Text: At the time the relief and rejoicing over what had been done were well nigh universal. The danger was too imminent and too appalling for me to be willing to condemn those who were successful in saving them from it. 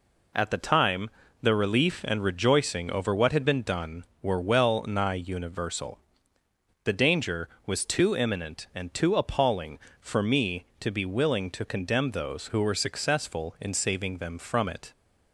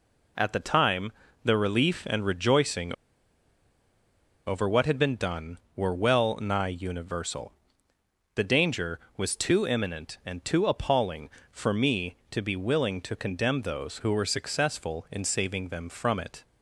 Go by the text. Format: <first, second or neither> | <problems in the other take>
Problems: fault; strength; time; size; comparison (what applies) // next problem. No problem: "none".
first | pauses between "time" and "the"; slight; at 1.1 s; 0.32 s long; slight in the first // pauses between "rejoicing" and "over"; strong; at 2.9 s; 1.5 s long